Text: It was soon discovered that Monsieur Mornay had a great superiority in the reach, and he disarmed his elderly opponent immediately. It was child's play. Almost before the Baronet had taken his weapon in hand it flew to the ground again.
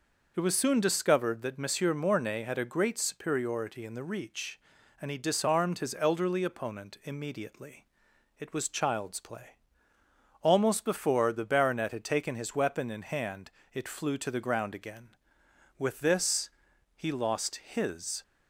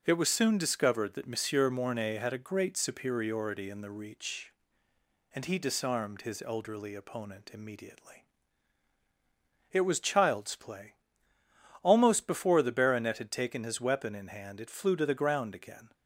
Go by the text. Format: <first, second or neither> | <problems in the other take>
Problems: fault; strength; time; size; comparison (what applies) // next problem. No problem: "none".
second | pauses between "hand" and "it"; slight; at 13.5 s; 0.24 s long // goes on to say "With this he lost his"; strong; from 15.7 s on; 2.4 s long